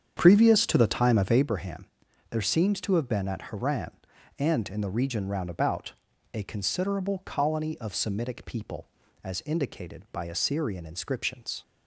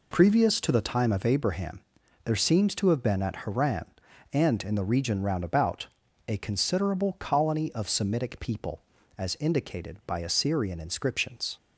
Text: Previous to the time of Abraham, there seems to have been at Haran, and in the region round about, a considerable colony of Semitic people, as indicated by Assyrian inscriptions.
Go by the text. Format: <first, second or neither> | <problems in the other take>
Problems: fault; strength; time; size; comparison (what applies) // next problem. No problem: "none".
second | starts louder than the rest; strong; until 1.5 s; 8 dB